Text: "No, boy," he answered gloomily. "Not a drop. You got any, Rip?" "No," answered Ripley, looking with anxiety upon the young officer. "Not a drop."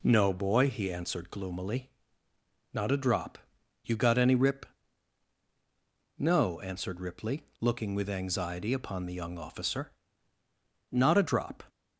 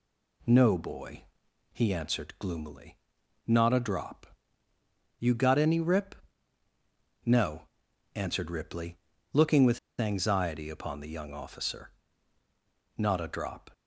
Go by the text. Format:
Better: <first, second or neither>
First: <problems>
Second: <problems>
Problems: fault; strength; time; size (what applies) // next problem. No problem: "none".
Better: first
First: none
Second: pauses between "with" and "anxiety"; slight; at 9.7 s; 0.19 s long